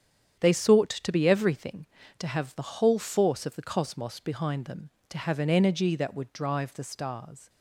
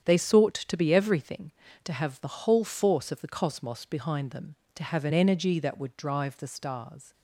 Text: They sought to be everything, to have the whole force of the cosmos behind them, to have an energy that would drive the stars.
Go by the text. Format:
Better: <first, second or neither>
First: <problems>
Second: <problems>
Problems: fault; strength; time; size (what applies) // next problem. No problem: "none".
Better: neither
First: starts louder than the rest; strong; until 1.4 s; 8.5 dB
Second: starts louder than the rest; strong; until 1.0 s; 8.5 dB